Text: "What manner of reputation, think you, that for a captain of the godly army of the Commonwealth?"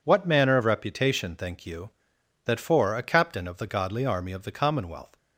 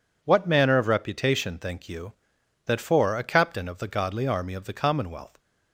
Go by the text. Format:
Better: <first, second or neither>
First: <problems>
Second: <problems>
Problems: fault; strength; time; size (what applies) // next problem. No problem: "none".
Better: neither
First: none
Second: none